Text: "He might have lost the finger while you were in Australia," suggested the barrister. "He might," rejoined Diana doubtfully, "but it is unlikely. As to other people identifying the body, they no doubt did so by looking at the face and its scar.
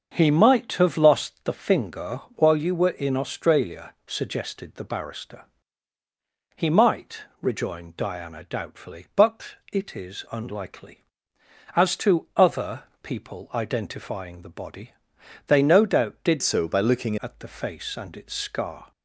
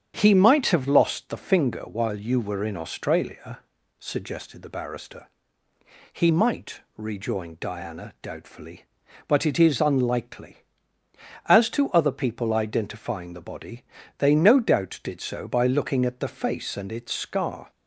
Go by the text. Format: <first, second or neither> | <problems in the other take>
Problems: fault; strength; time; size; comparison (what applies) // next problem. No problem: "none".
second | starts louder than the rest; until 1.1 s; 7 dB; strong in the second // pauses between "but" and "it"; slight; at 9.5 s; 0.18 s long // pauses between "other" and "people"; slight; at 12.8 s; 0.18 s long // changes voice from "so" to "looking"; from 16.4 to 17.1 s; 0.7 s long